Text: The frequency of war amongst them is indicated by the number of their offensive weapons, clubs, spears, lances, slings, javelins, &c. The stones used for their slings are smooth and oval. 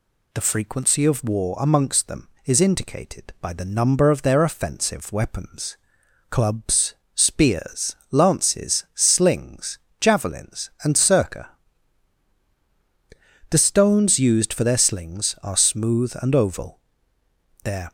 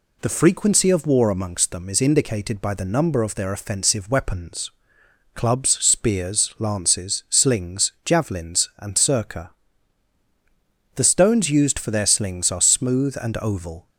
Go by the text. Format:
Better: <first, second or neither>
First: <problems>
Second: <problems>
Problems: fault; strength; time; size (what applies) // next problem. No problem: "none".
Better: second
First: goes on to say "Their"; slight; from 17.6 s on; 0.28 s long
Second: none